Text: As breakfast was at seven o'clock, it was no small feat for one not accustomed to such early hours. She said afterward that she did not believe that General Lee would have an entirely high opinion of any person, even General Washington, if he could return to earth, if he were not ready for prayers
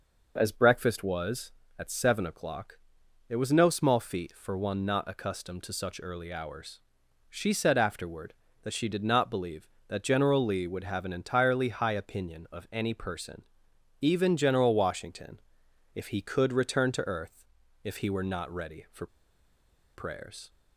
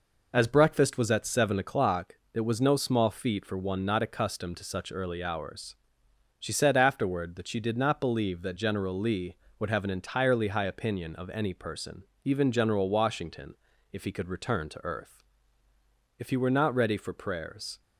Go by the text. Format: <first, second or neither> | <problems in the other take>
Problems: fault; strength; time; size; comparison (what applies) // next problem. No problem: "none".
second | pauses between "for" and "prayers"; noticeable; at 19.0 s; 0.88 s long